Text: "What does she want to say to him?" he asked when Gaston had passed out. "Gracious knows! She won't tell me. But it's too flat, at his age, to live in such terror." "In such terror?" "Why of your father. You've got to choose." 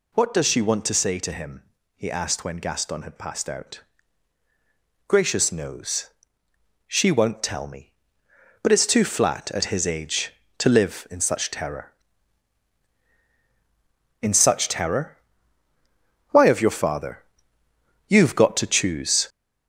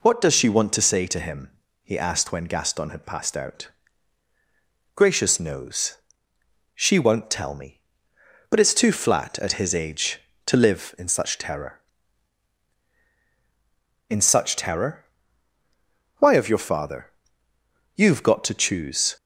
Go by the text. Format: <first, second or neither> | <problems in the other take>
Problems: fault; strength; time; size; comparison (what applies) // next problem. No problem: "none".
second | gets louder; noticeable; throughout; 5 dB